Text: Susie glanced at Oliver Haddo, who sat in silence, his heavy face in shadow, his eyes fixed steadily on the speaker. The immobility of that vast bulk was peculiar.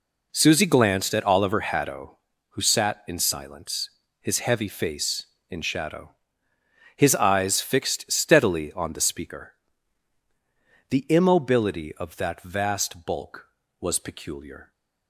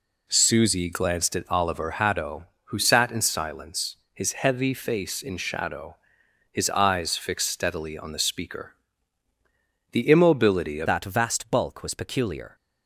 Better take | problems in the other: first | changes voice at "that"; from 10.8 s on; 1.7 s long

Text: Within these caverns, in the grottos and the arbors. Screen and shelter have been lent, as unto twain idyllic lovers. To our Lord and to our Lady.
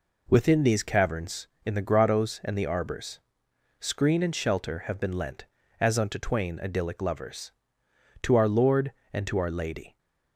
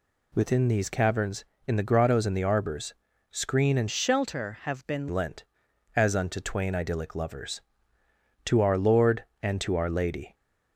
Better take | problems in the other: first | changes voice from "shelter" to "been"; from 3.9 to 5.0 s; 1.1 s long

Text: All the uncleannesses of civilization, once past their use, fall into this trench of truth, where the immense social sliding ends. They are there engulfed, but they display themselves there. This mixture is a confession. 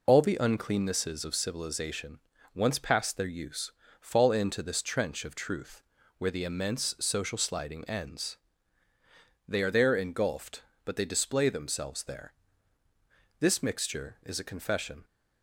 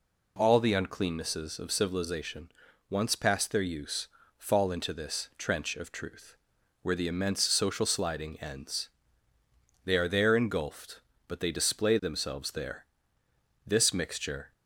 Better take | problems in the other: first | stops before "is a confession"; at 14.5 s

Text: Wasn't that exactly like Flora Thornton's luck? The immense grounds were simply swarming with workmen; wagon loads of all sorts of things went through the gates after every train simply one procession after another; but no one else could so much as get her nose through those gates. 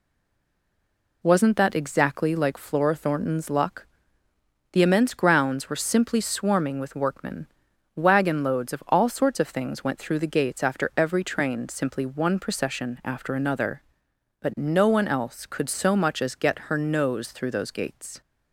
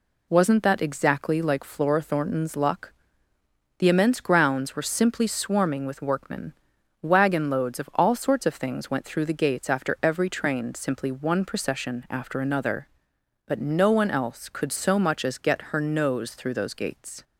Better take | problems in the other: second | stays silent before the first word; noticeable; until 1.2 s; 1.2 s long

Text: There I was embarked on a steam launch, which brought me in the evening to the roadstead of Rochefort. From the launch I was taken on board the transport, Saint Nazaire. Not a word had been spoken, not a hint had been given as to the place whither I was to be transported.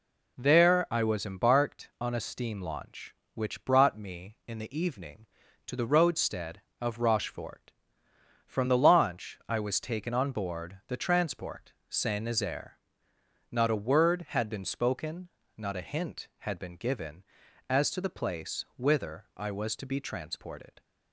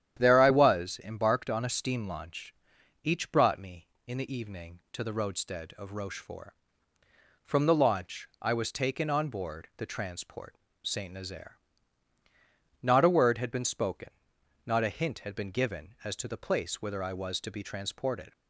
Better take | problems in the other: first | starts louder than the rest; strong; until 1.2 s; 10 dB // says "each" for "which"; at 3.0 s

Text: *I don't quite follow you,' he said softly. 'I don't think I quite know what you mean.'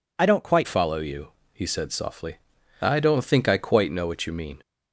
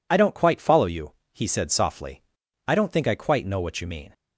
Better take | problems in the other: second | changes voice at "follow"; from 0.6 s on; 4.0 s long

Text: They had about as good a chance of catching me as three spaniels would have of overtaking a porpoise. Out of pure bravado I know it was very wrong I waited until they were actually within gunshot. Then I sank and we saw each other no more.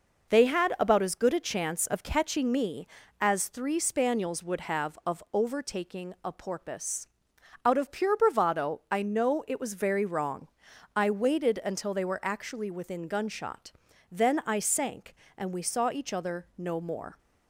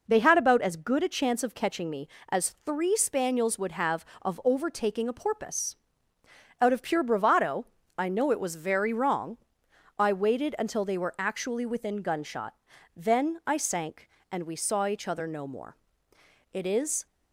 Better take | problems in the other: first | pauses between "bravado" and "I"; slight; at 7.6 s; 0.32 s long // pauses between "wrong" and "I"; noticeable; at 9.3 s; 0.60 s long; noticeable in the first // goes on to say "It is"; from 16.5 s on; 0.54 s long

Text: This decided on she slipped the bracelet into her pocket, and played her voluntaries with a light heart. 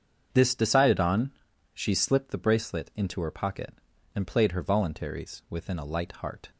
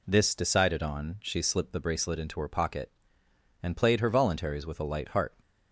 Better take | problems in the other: second | starts louder than the rest; strong; until 1.3 s; 7.5 dB // pauses between "on" and "she"; at 1.3 s; 0.42 s long // says "within" for "with"; at 5.5 s

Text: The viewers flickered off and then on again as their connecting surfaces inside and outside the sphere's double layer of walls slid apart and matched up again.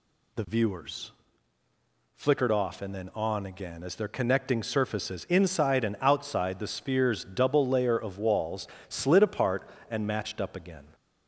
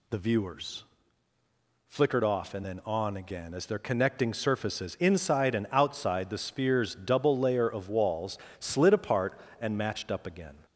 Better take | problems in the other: neither | pauses between "viewers" and "flickered"; the same in both // pauses between "walls" and "slid"; slight; the same in both

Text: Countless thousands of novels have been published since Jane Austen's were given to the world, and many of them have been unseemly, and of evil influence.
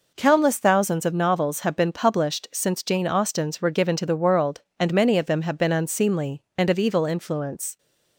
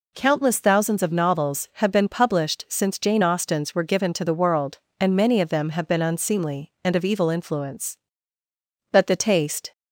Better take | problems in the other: first | goes on to say "But the taste"; noticeable; from 8.9 s on; 0.80 s long

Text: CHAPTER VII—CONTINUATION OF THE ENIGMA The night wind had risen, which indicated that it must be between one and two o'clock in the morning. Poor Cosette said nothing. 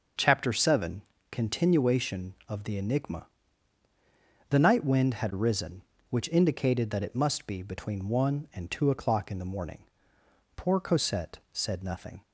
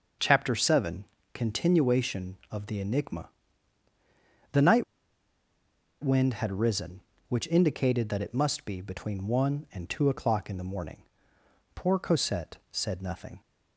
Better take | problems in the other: first | starts louder than the rest; until 1.4 s; 6 dB; also in the first // pauses between "ENIGMA" and "The"; at 3.2 s; 1.2 s long; also in the first // pauses between "night" and "wind"; at 4.8 s; 1.1 s long // pauses between "Cosette" and "said"; slight; at 12.5 s; 0.16 s long; slight in the first

